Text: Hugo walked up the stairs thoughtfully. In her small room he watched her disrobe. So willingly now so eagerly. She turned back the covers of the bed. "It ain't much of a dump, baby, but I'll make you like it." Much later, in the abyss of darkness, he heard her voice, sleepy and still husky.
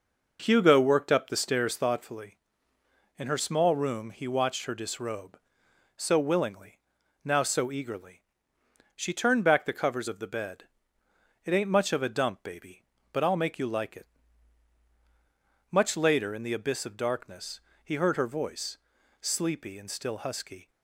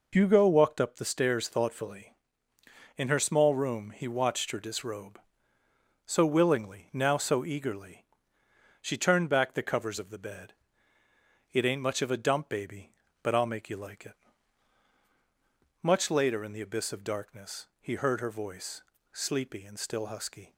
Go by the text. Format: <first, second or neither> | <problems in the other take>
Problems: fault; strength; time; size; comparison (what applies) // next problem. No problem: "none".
second | says "worked" for "walked"; at 0.8 s // pauses between "willingly" and "now"; at 6.7 s; 0.44 s long